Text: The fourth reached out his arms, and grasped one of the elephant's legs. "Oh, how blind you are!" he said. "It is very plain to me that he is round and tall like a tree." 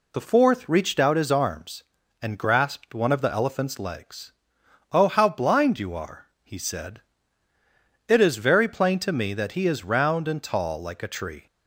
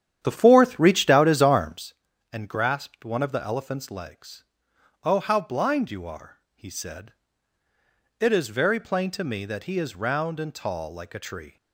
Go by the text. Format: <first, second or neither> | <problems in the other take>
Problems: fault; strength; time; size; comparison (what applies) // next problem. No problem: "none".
first | starts louder than the rest; strong; until 1.9 s; 10 dB